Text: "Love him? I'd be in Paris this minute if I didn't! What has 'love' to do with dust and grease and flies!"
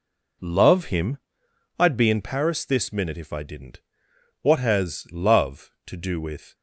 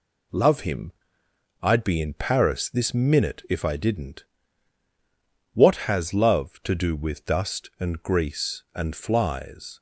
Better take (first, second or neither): second